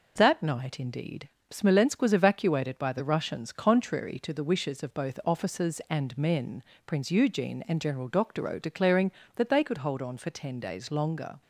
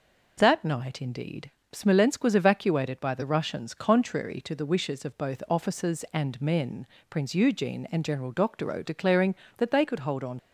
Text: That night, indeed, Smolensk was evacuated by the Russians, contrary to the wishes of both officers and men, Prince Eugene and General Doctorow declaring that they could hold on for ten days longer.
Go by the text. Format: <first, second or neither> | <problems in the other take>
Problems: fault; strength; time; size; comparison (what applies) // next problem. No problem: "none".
first | stops before "for ten days longer"; at 10.3 s